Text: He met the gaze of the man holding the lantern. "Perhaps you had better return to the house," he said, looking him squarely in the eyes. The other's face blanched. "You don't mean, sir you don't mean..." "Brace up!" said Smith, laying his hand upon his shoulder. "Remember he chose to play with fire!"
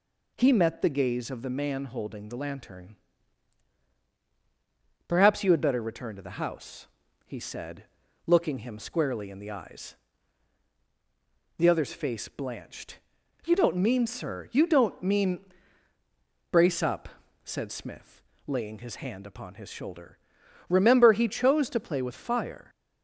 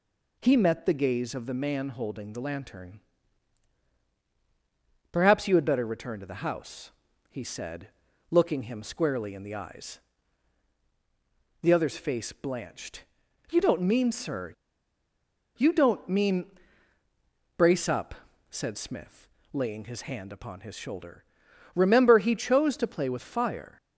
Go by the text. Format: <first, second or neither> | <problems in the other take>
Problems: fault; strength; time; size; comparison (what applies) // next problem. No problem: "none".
first | pauses between "sir" and "you"; at 14.5 s; 1.0 s long